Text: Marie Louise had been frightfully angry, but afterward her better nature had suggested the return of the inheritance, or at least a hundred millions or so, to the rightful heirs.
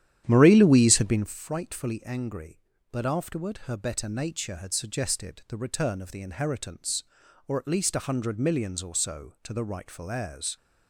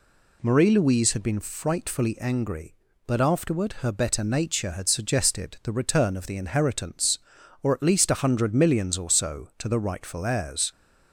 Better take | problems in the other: second | starts louder than the rest; strong; until 1.4 s; 10.5 dB

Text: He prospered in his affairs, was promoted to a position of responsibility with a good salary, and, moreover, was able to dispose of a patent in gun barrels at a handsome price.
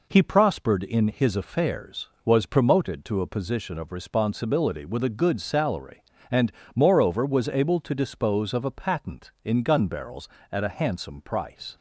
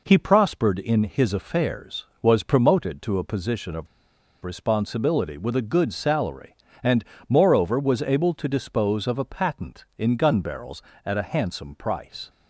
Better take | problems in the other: first | pauses between "of" and "responsibility"; noticeable; at 3.8 s; 0.56 s long

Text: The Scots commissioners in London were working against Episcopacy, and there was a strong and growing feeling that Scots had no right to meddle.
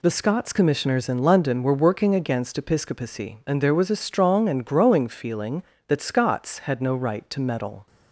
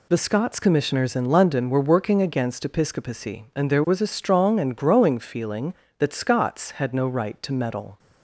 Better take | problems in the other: neither | none

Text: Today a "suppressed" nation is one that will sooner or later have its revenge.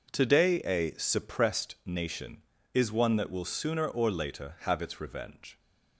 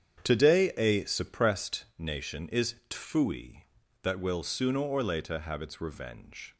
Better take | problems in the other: first | starts louder than the rest; strong; until 1.2 s; 8.5 dB // says "tfui" for "one"; at 2.9 s

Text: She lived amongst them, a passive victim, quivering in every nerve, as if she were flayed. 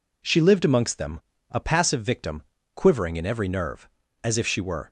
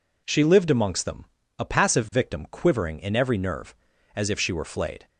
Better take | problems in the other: second | stops before "flayed"; at 4.8 s

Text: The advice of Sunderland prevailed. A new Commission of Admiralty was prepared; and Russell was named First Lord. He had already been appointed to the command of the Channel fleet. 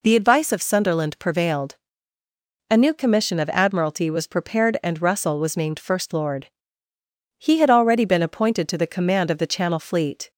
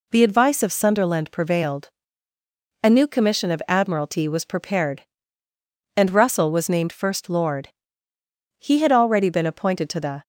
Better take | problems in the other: first | stops before "command of the Channel fleet"; at 10.2 s

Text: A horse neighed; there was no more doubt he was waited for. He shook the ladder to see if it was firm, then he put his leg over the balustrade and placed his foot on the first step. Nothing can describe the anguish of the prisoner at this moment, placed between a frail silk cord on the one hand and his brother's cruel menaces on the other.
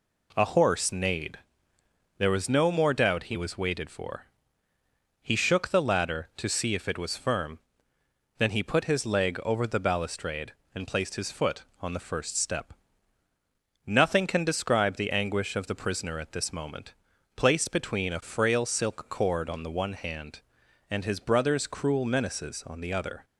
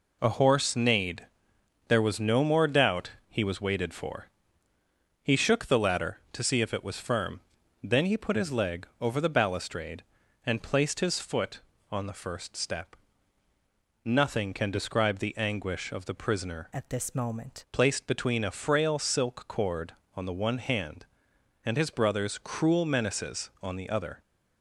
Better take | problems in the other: first | pauses between "doubt" and "he"; slight; at 3.1 s; 0.16 s long // pauses between "leg" and "over"; slight; at 8.8 s; 0.16 s long // changes voice from "at" to "moment"; from 16.7 to 17.6 s; 0.9 s long

